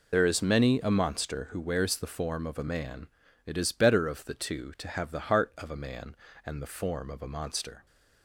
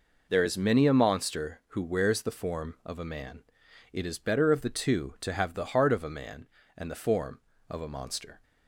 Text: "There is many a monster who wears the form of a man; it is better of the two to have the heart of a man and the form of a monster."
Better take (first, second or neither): second